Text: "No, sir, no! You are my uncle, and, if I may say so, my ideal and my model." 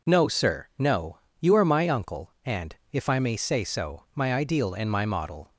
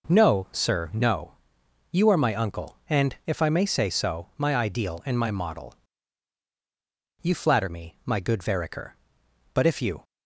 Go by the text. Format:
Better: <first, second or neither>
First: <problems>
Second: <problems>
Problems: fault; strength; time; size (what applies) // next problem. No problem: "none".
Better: first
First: none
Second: goes on to say "You flatter me my good Vereker But if you"; strong; from 7.2 s on; 2.8 s long